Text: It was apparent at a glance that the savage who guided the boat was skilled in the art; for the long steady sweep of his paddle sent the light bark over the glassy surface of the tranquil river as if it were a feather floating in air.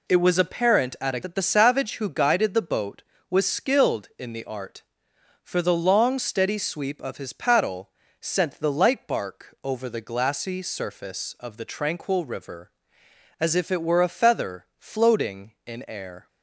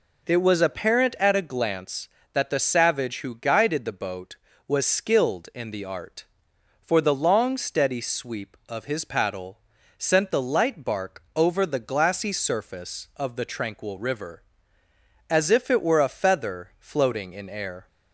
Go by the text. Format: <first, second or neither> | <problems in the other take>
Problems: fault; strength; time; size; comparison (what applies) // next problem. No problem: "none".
second | skips "glance"; at 1.2 s // pauses between "paddle" and "sent"; slight; at 7.9 s; 0.28 s long; also in the second